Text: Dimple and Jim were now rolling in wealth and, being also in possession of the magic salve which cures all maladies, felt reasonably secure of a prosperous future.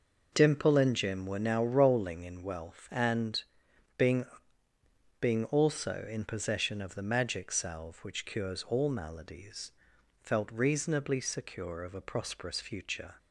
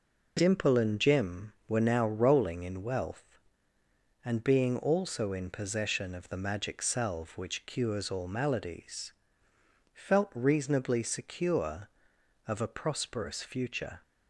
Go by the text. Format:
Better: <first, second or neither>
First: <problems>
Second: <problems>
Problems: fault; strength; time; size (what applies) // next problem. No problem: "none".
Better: second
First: says "being" twice; at 5.1 s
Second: none